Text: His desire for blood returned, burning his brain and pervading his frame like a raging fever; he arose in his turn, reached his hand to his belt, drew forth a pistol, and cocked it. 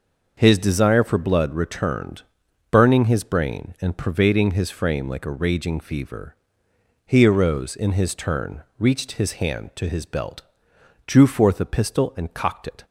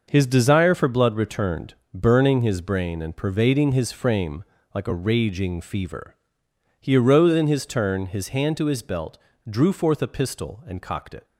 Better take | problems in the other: first | starts louder than the rest; noticeable; until 1.0 s; 6 dB // pauses between "frame" and "like"; slight; at 4.4 s; 0.30 s long // skips "reached"; at 8.0 s

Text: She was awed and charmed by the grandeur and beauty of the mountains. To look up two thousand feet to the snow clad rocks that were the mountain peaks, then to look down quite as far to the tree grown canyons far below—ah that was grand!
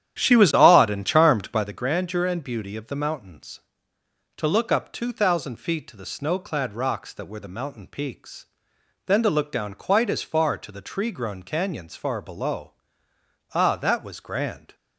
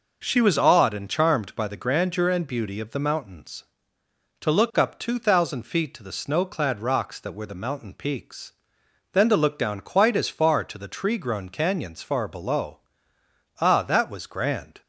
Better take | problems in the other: second | starts louder than the rest; strong; until 1.8 s; 10.5 dB

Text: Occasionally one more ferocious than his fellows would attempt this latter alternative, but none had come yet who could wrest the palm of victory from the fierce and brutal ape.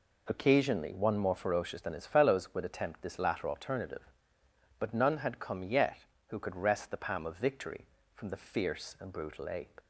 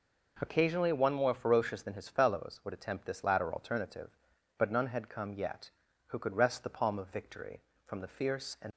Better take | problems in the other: first | stops before "brutal ape"; at 8.7 s

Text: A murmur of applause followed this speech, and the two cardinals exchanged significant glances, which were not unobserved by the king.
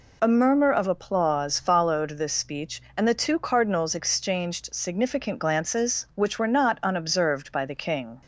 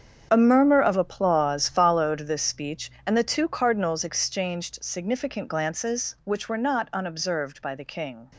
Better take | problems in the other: first | gets quieter; strong; throughout; 13.5 dB

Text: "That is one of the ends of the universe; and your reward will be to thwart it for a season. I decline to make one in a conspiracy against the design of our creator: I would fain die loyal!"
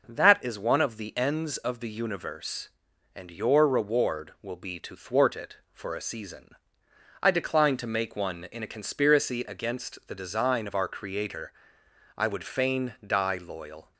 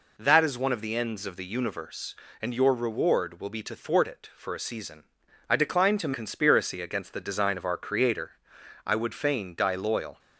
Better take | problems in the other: first | skips "make one in a"; at 6.1 s

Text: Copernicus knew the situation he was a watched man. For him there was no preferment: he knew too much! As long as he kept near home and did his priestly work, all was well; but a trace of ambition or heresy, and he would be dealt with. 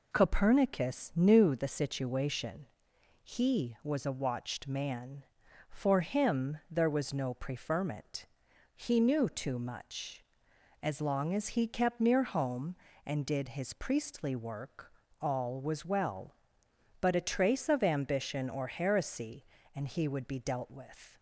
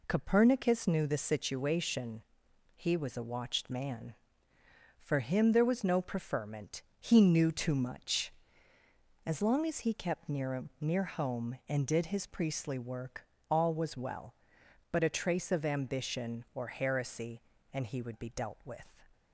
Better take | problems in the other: first | pauses between "situation" and "he"; noticeable; at 2.2 s; 0.54 s long; noticeable in the first // says "near" twice; at 10.7 s

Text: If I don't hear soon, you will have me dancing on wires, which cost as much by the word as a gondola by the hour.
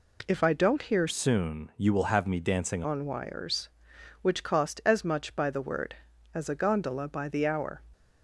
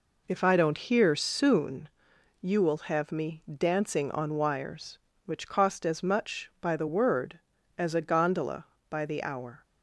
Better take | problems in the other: second | changes voice from "soon" to "dancing"; from 1.0 to 2.8 s; 1.8 s long

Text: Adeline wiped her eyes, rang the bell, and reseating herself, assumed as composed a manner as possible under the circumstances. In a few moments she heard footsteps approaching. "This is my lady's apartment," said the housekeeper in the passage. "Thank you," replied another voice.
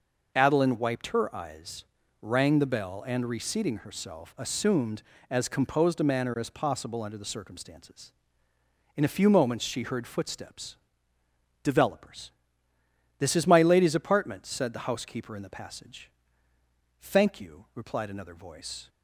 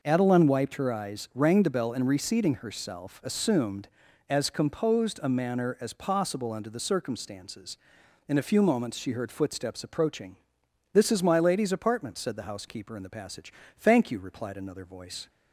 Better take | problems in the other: second | says "developers" for "approaching"; at 11.6 s

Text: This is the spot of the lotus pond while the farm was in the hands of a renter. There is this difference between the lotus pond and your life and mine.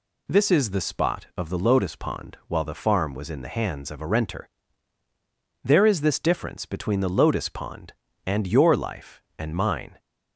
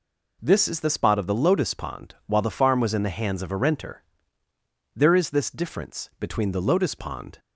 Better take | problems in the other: first | stops before "and your life and mine"; at 7.3 s

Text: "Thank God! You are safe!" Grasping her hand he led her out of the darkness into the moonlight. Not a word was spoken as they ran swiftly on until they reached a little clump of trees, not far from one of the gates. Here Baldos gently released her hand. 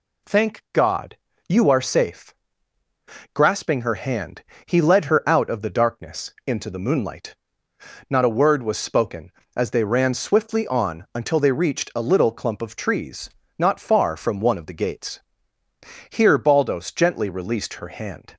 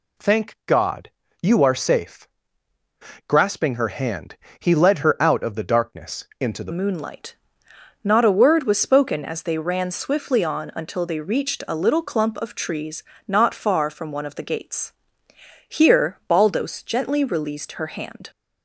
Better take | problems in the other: first | pauses between "hand" and "he"; slight; at 4.3 s; 0.24 s long; slight in the first // changes voice at "moonlight"; from 6.7 s on; 11.6 s long

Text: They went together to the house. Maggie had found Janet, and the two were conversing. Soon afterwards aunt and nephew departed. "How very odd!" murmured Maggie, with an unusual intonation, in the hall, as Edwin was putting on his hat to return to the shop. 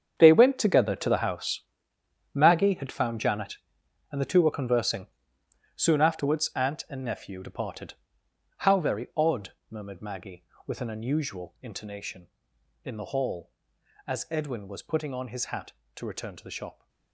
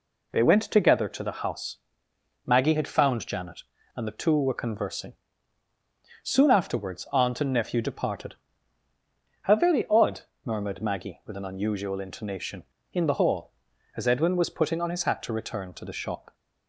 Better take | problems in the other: second | gets quieter; strong; throughout; 14.5 dB

